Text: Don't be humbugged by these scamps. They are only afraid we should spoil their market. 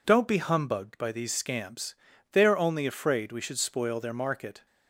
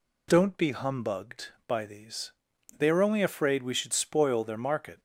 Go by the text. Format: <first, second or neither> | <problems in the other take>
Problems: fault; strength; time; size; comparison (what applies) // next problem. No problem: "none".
first | skips "scamps"; at 2.5 s